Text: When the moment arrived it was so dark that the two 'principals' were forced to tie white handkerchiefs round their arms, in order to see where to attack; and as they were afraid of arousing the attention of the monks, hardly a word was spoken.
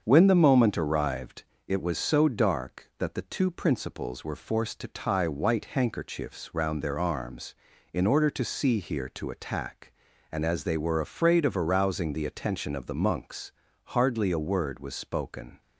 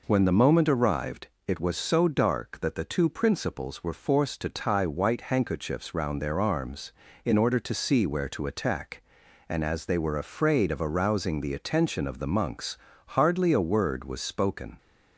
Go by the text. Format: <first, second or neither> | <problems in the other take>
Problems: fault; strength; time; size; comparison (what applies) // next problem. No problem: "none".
second | starts louder than the rest; until 1.0 s; 7 dB // pauses between "arrived" and "it"; slight; at 1.4 s; 0.24 s long; slight in the second // says "here" for "where"; at 8.8 s